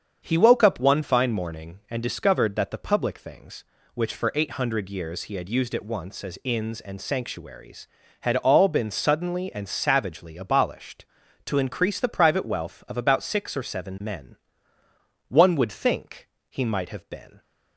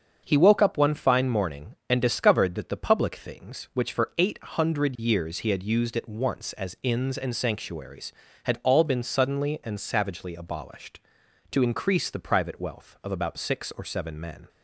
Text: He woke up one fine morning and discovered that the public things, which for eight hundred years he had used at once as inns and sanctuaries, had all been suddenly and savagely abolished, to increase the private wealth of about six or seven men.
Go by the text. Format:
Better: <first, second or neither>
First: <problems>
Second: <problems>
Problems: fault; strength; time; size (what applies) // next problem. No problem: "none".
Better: second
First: starts louder than the rest; strong; until 1.2 s; 7.5 dB // goes on to say "One would think he might have been"; strong; from 15.2 s on; 2.1 s long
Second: starts louder than the rest; until 1.2 s; 7 dB